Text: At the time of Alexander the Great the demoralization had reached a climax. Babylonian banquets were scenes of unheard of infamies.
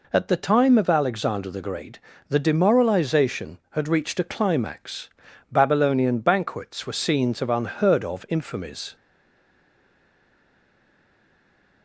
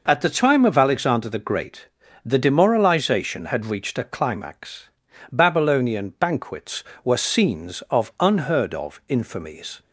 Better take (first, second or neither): second